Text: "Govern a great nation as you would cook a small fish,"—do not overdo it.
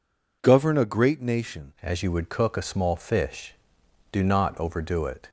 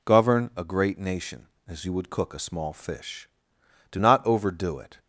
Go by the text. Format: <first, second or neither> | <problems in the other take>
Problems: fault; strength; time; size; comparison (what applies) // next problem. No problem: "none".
second | changes voice at "as"; from 1.8 s on; 3.4 s long